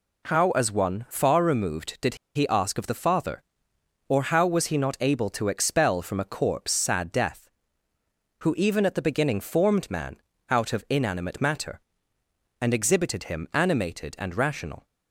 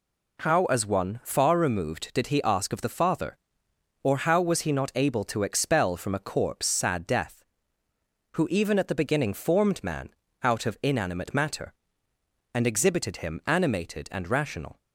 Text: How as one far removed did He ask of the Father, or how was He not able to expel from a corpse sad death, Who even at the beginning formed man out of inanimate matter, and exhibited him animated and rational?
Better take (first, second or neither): second